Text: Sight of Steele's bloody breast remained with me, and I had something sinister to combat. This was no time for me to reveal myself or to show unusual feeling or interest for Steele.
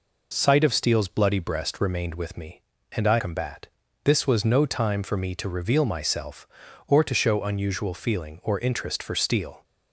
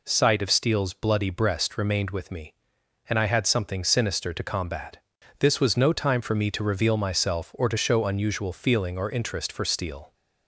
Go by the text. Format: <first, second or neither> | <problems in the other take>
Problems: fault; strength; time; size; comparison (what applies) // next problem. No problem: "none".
second | skips "had something sinister to"; at 3.1 s